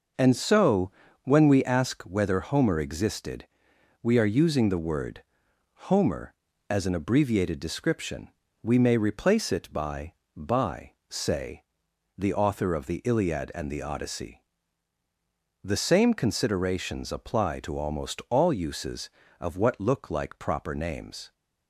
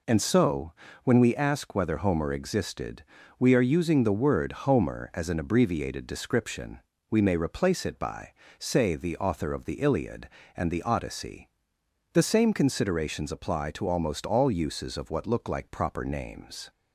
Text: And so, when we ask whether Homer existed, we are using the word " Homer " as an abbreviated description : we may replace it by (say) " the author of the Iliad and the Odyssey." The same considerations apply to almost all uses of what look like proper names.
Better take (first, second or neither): second